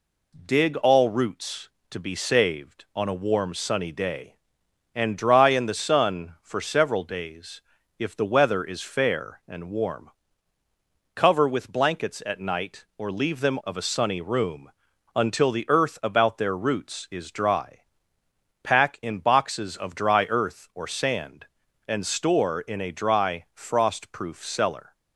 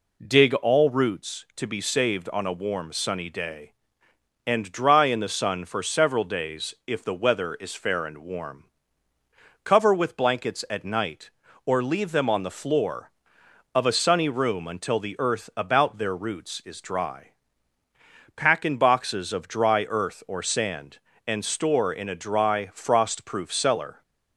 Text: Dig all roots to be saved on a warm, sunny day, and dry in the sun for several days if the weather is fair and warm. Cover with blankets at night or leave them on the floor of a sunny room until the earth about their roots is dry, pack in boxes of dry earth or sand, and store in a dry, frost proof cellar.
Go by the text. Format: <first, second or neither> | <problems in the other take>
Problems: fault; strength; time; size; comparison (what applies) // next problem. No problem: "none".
second | pauses between "days" and "if"; slight; at 7.6 s; 0.36 s long // skips "on the floor"; at 13.6 s // pauses between "room" and "until"; at 14.7 s; 0.44 s long